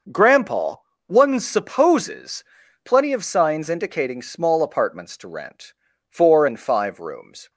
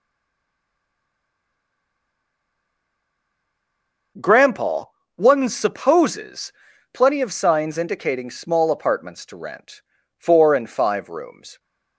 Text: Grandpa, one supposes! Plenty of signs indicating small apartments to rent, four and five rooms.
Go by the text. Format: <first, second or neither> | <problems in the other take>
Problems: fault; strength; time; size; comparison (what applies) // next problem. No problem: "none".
first | stays silent before the first word; strong; until 4.1 s; 4.1 s long